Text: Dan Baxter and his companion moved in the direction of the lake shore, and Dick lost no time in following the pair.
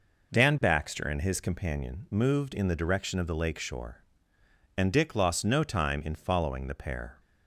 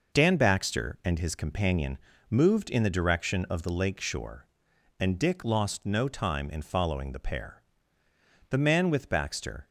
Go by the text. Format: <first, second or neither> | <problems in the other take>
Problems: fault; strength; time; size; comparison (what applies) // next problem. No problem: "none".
first | pauses between "companion" and "moved"; slight; at 1.9 s; 0.32 s long // goes on to say "The man with Baxter"; noticeable; from 8.4 s on; 1.1 s long